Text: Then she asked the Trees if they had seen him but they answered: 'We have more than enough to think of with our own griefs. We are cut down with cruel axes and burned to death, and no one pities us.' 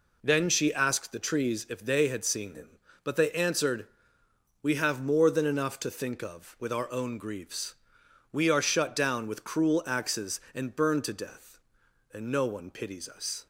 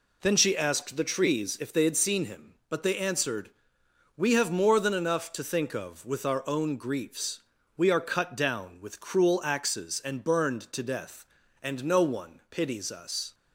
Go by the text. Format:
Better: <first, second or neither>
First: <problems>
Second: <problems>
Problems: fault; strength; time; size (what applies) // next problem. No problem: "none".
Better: second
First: says "shut" for "cut"; at 8.6 s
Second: none